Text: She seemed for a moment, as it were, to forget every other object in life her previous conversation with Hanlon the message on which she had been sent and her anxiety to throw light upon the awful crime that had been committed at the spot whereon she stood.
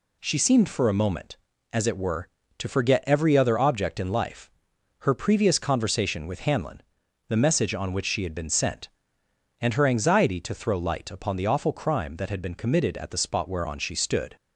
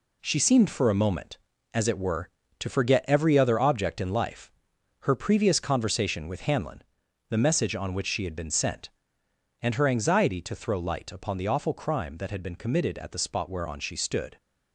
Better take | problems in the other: first | gets quieter; strong; throughout; 7 dB // pauses between "life" and "her"; noticeable; at 4.5 s; 0.54 s long; noticeable in the first // pauses between "Hanlon" and "the"; noticeable; at 6.8 s; 0.48 s long; noticeable in the first

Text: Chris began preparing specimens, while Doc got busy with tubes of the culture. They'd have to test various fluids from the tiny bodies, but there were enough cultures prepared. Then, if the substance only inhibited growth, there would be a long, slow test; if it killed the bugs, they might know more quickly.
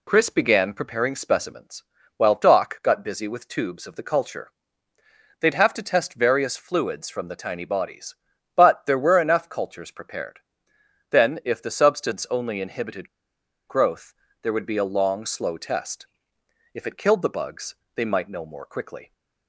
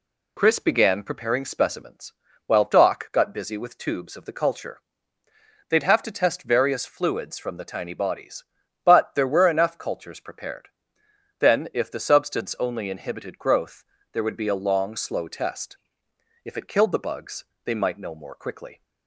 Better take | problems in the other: second | pauses between "inhibited" and "growth"; noticeable; at 13.0 s; 0.60 s long

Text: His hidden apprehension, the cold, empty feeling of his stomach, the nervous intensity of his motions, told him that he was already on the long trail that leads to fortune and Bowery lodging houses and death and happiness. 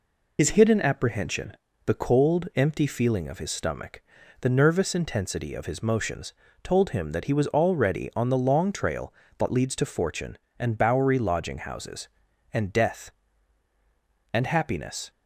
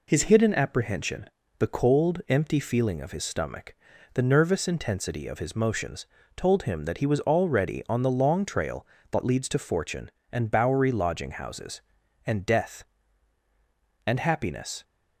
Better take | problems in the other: second | loses the start of "His"; at 0.3 s; 40 ms

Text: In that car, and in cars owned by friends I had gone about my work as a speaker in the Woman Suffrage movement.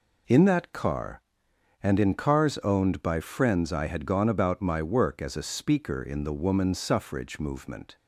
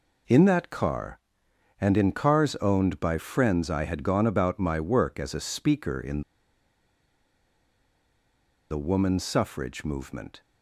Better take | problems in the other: first | pauses between "in" and "the"; strong; at 6.2 s; 2.4 s long

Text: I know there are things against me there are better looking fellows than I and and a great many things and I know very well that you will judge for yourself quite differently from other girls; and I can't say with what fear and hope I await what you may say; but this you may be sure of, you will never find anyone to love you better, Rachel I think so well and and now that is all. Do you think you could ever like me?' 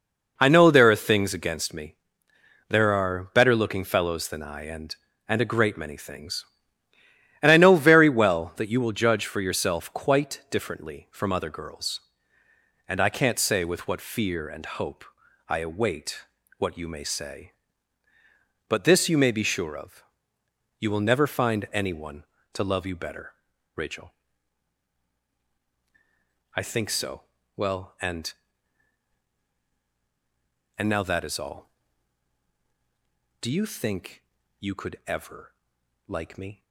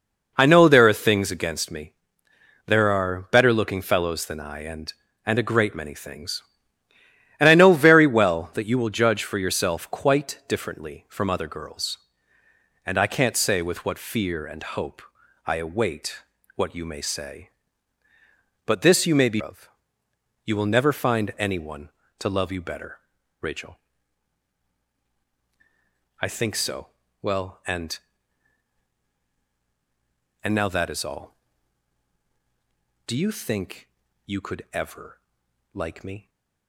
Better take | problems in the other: first | pauses between "me" and "there"; noticeable; at 1.9 s; 0.72 s long; noticeable in the first // pauses between "hope" and "I"; at 15.0 s; 0.44 s long; also in the first // pauses between "await" and "what"; slight; at 16.2 s; 0.34 s long; slight in the first // skips "sure"; at 19.4 s // pauses between "Rachel" and "I"; strong; at 23.7 s; 2.4 s long; strong in the first // pauses between "so" and "well"; slight; at 26.8 s; 0.34 s long; slight in the first // pauses between "think" and "you"; at 33.8 s; 0.38 s long; also in the first // pauses between "ever" and "like"; noticeable; at 35.1 s; 0.56 s long; noticeable in the first

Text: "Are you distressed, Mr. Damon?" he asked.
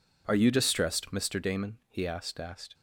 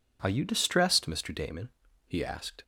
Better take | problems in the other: second | says "asked" twice; at 2.3 s

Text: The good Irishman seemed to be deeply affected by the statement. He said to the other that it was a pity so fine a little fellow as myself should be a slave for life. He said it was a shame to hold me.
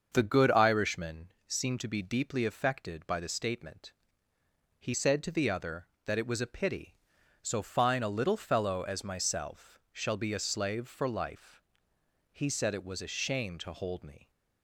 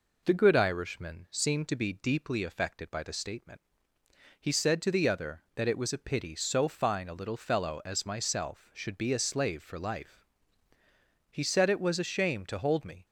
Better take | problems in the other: second | starts louder than the rest; until 1.1 s; 6.5 dB // pauses between "Irishman" and "seemed"; slight; at 1.3 s; 0.16 s long // says "shall" for "should"; at 9.9 s

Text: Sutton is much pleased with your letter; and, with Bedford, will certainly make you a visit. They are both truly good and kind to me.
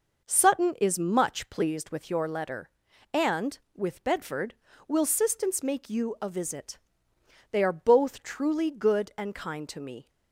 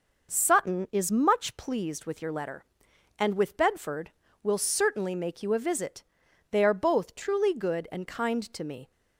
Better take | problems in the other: second | says "sistance" for "certainly"; at 5.0 s

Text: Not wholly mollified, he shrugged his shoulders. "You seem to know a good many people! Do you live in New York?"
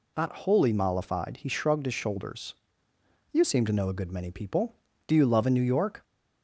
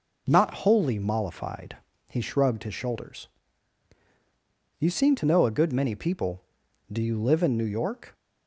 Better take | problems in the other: second | says "love" for "live"; at 5.2 s

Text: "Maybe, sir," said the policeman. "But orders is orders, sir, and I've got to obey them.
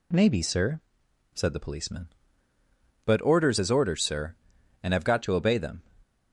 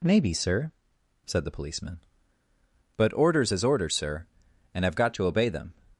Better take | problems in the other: neither | none

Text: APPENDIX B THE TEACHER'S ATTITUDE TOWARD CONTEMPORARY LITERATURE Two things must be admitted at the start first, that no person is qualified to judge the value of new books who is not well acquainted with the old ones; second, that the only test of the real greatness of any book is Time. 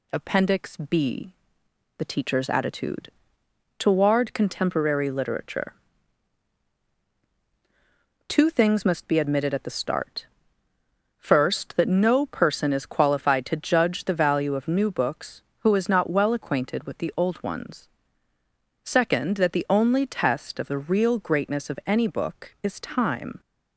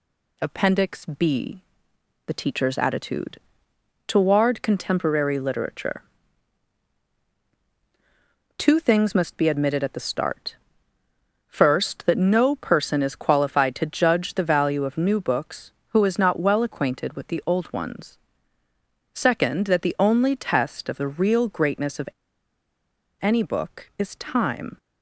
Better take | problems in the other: first | pauses between "B" and "THE"; noticeable; at 1.6 s; 0.66 s long; noticeable in the first // pauses between "ATTITUDE" and "TOWARD"; noticeable; at 3.3 s; 0.66 s long; noticeable in the first // pauses between "LITERATURE" and "Two"; strong; at 6.0 s; 2.5 s long; strong in the first // pauses between "start" and "first"; noticeable; at 10.5 s; 0.92 s long; noticeable in the first // pauses between "of" and "any"; at 22.0 s; 1.1 s long

